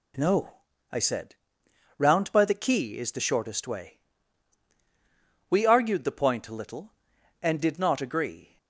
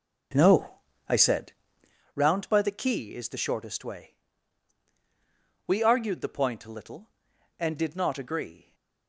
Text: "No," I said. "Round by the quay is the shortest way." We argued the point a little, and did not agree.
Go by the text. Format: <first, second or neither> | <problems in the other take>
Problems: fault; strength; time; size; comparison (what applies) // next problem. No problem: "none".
first | starts louder than the rest; noticeable; until 2.0 s; 5 dB